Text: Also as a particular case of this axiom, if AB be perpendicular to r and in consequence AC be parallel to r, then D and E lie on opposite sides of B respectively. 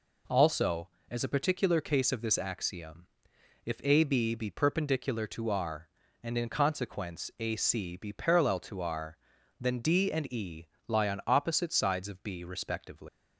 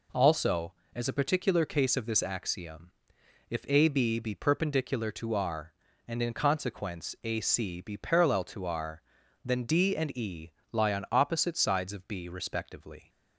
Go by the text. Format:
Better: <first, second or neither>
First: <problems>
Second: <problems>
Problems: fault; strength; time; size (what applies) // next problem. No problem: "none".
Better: second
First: pauses between "E" and "lie"; slight; at 10.6 s; 0.22 s long // leaves "respectively" unfinished; at 13.0 s; 155 ms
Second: pauses between "E" and "lie"; slight; at 10.5 s; 0.22 s long